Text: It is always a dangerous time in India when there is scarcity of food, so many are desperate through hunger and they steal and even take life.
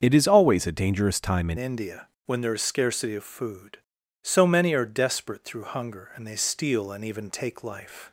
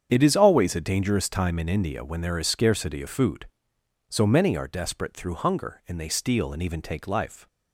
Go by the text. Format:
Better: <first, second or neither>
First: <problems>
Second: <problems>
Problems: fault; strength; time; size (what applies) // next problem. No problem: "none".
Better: second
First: starts louder than the rest; until 1.0 s; 7 dB // changes voice at "India"; from 1.5 s on; 6.6 s long // pauses between "India" and "when"; slight; at 2.0 s; 0.20 s long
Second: starts louder than the rest; strong; until 1.1 s; 8 dB